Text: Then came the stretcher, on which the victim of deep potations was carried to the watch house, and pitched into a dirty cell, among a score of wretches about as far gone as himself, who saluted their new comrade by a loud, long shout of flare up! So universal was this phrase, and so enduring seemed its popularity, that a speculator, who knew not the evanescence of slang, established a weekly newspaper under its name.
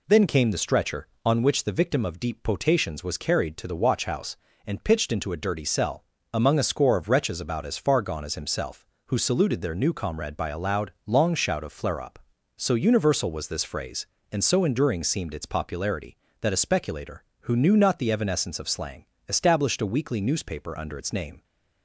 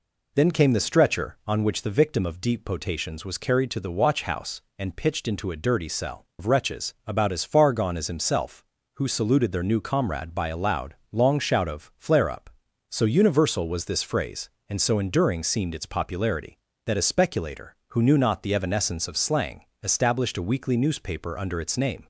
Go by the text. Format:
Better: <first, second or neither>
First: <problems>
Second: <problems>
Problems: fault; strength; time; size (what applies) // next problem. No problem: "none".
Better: first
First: none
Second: skips "among a score"; at 6.3 s